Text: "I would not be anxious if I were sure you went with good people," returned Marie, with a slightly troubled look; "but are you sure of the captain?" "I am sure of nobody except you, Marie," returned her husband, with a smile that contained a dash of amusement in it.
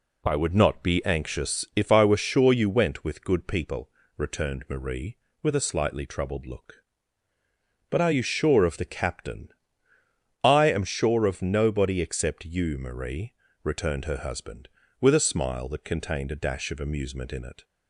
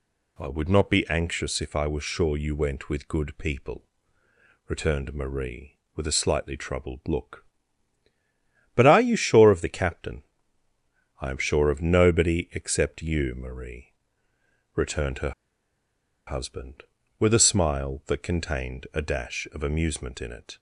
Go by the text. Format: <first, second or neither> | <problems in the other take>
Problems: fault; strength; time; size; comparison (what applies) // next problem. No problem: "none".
first | pauses between "her" and "husband"; noticeable; at 15.3 s; 0.95 s long